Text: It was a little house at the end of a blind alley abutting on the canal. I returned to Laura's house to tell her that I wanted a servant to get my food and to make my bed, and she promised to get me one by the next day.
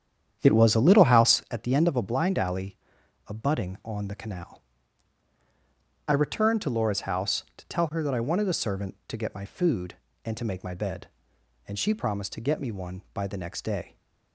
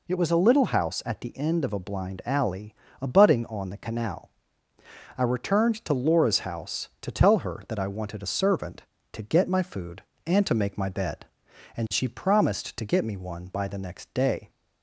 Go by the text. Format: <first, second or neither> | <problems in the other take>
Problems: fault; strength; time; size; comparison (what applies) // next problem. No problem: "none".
second | starts louder than the rest; strong; until 1.4 s; 9 dB // pauses between "alley" and "abutting"; noticeable; at 2.7 s; 0.50 s long; slight in the second